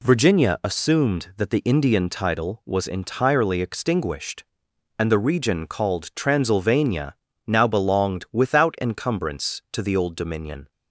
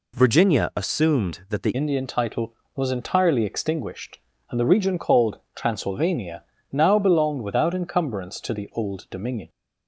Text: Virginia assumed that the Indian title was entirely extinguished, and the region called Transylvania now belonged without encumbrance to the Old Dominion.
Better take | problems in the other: first | changes voice at "Indian"; from 1.7 s on; 7.7 s long // pauses between "called" and "Transylvania"; slight; at 5.3 s; 0.16 s long // pauses between "Transylvania" and "now"; slight; at 6.4 s; 0.28 s long; slight in the first

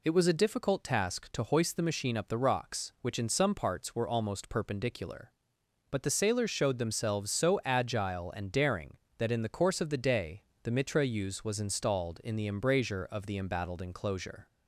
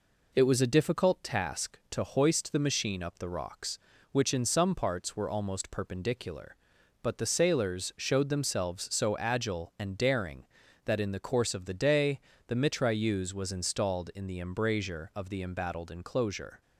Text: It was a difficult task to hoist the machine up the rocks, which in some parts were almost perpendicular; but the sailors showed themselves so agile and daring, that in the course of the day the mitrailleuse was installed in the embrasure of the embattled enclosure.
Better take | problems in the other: neither | pauses between "day" and "the"; slight; the same in both

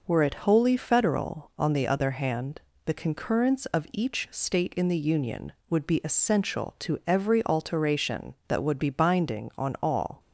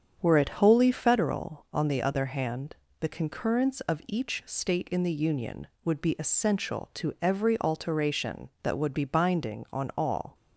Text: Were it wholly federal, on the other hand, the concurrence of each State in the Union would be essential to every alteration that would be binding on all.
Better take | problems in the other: first | starts louder than the rest; strong; until 1.2 s; 7.5 dB

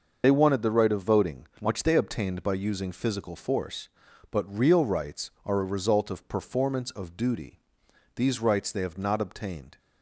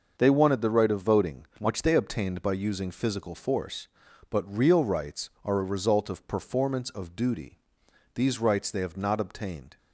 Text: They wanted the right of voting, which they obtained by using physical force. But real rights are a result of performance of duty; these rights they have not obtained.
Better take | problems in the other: second | loses the start of "They"; at 0.2 s; 40 ms // starts louder than the rest; noticeable; until 1.2 s; 6 dB; also in the second

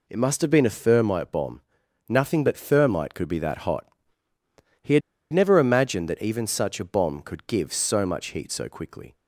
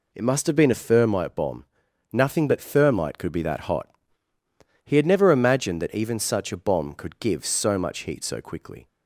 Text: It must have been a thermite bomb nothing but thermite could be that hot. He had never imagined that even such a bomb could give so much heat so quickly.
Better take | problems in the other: second | pauses between "bomb" and "nothing"; noticeable; at 1.6 s; 0.46 s long; noticeable in the second // pauses between "had" and "never"; slight; at 5.0 s; 0.31 s long

